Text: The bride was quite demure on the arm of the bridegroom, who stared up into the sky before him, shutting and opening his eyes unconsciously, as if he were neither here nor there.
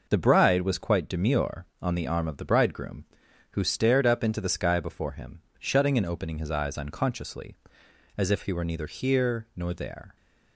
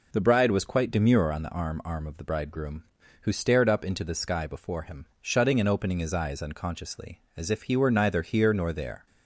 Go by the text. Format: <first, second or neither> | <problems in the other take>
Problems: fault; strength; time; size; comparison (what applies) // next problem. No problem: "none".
first | says "arm" twice; at 1.8 s